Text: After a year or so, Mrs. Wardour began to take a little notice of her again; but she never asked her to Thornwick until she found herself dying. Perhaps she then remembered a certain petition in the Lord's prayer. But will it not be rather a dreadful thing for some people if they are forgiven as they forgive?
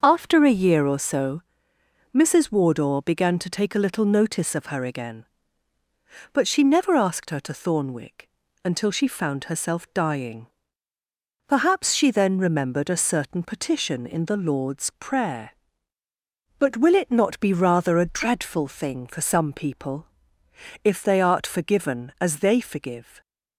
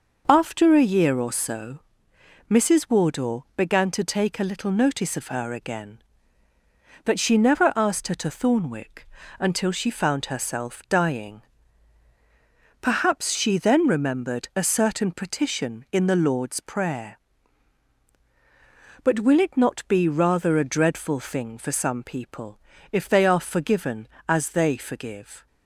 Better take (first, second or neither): second